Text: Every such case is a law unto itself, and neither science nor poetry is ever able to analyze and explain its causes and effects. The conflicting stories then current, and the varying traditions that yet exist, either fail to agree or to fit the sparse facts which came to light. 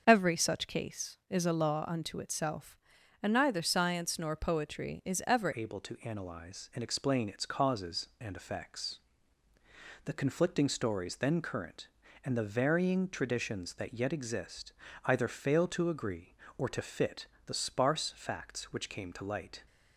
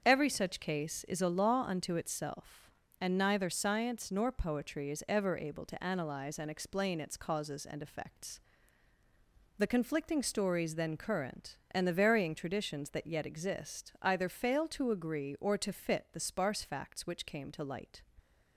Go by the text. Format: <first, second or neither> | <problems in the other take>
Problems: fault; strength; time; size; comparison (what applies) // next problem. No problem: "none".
second | starts louder than the rest; until 1.0 s; 6.5 dB; strong in the second // changes voice at "able"; from 5.5 s on; 14.1 s long // pauses between "fit" and "the"; slight; at 17.2 s; 0.18 s long